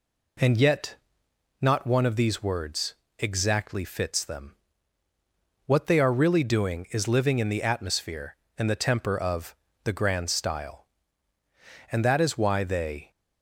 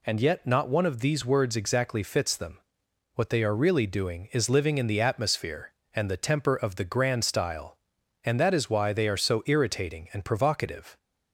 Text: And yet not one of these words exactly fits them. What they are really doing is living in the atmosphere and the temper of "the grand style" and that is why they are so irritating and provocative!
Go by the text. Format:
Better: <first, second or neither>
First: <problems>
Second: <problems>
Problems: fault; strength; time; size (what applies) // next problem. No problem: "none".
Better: second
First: pauses between "yet" and "not"; noticeable; at 0.9 s; 0.66 s long // pauses between "words" and "exactly"; slight; at 2.9 s; 0.24 s long // pauses between "of" and "the"; slight; at 9.5 s; 0.26 s long // stops before "are so irritating and provocative"; at 13.1 s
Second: none